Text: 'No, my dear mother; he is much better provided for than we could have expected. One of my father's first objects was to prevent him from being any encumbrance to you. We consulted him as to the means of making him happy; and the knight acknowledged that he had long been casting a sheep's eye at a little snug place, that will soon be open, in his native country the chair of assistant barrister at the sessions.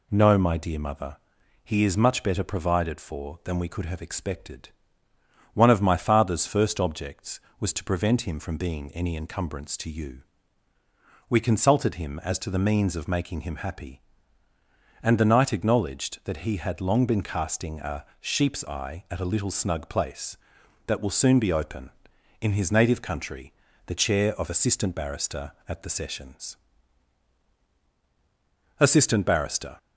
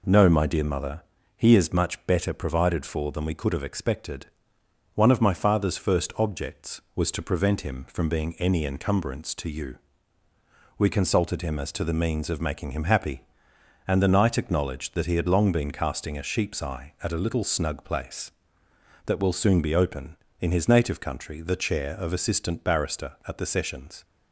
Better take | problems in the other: second | pauses between "country" and "the"; slight; at 23.5 s; 0.34 s long // goes on to say "Assistant barrister"; noticeable; from 28.7 s on; 0.98 s long

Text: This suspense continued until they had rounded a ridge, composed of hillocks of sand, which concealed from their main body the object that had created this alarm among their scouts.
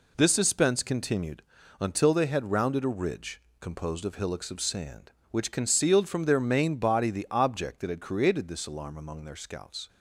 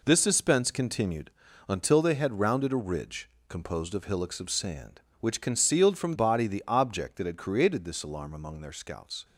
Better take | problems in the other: first | pauses between "continued" and "until"; at 1.2 s; 0.40 s long; also in the first // skips "their main"; at 6.1 s

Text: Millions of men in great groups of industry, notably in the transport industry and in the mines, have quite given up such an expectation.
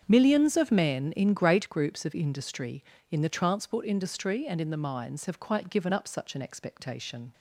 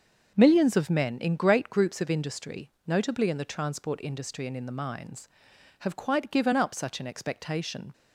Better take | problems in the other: second | starts louder than the rest; strong; until 1.0 s; 7.5 dB; also in the second // skips "notably"; at 2.9 s

